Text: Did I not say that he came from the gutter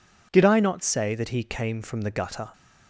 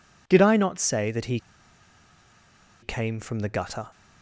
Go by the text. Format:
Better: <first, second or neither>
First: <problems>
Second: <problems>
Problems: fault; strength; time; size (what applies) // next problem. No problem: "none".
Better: first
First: none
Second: pauses between "he" and "came"; strong; at 1.3 s; 1.4 s long